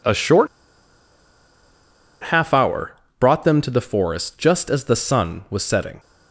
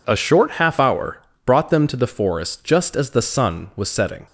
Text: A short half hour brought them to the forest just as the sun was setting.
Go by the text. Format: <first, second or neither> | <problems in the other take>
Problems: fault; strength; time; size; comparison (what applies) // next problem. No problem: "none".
second | pauses between "short" and "half"; strong; at 0.4 s; 1.8 s long // pauses between "hour" and "brought"; slight; at 2.9 s; 0.26 s long; slight in the second